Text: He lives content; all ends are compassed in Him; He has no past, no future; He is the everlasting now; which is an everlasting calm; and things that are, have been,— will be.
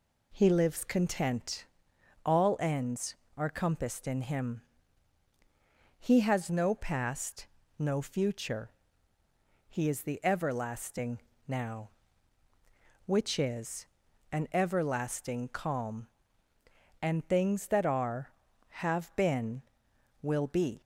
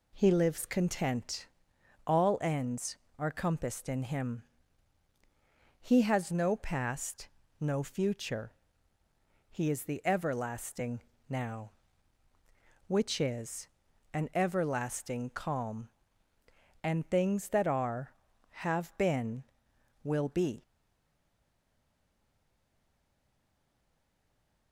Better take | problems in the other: first | pauses between "everlasting" and "now"; slight; at 10.9 s; 0.28 s long; slight in the first // pauses between "is" and "an"; noticeable; at 13.6 s; 0.46 s long; noticeable in the first // stays silent after the last word; strong; from 20.6 s on; 4.1 s long

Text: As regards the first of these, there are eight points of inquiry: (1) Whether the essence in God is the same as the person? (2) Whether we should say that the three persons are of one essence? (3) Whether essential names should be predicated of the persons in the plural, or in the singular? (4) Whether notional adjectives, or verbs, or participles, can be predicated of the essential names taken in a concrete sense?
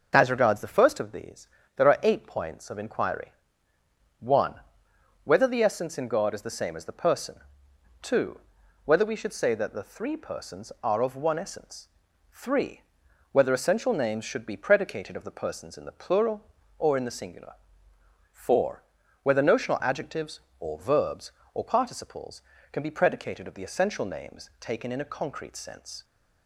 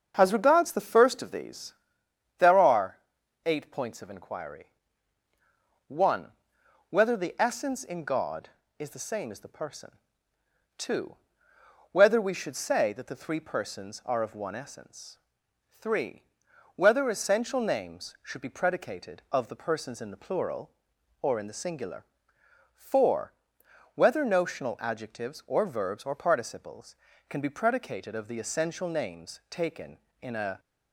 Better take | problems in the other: first | starts louder than the rest; until 1.1 s; 6.5 dB // pauses between "are" and "eight"; noticeable; at 2.9 s; 0.46 s long // stops before "concrete sense"; at 30.5 s

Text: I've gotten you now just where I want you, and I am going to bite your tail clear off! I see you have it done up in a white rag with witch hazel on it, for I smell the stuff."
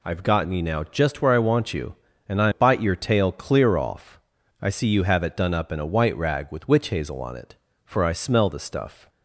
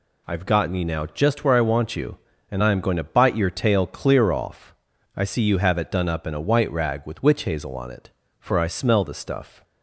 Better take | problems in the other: second | skips "am going to"; at 2.5 s

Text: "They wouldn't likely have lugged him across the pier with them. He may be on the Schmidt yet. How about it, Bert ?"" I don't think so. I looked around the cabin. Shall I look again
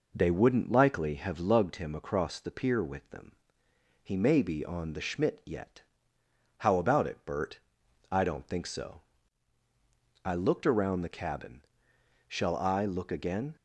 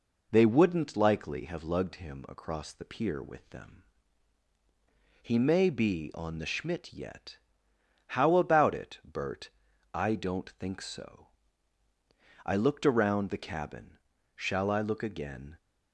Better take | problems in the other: neither | none

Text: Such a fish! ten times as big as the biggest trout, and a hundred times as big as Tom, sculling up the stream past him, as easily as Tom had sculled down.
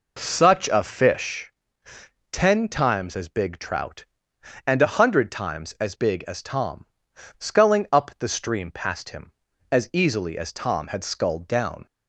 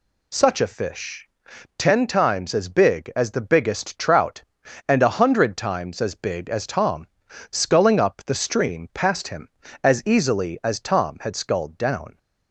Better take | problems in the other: second | skips "as the biggest"; at 3.5 s

